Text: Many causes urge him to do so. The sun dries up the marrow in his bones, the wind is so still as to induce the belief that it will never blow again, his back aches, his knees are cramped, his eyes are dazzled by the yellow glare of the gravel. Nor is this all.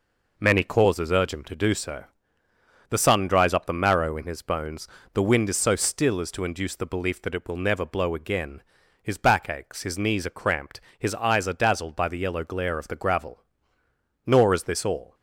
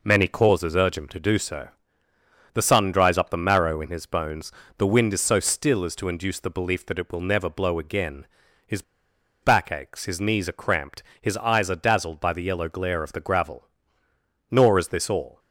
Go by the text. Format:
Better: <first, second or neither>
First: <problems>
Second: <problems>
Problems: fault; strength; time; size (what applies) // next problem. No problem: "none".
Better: first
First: none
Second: pauses between "his" and "back"; noticeable; at 8.8 s; 0.60 s long